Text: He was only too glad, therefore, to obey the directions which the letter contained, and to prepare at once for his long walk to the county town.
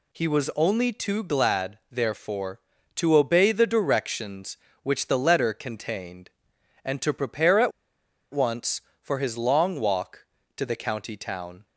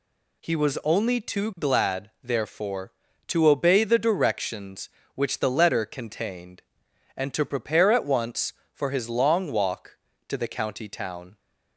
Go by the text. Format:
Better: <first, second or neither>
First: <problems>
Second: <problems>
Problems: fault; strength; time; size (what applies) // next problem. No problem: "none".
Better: second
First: pauses between "at" and "once"; noticeable; at 7.7 s; 0.61 s long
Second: none